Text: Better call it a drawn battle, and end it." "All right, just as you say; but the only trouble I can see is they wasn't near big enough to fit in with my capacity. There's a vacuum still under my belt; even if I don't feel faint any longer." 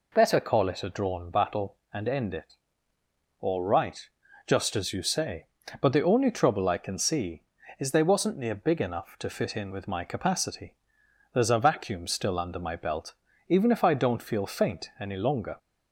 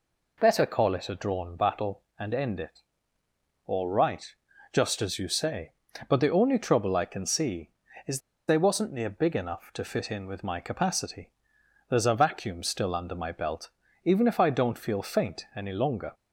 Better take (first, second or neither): first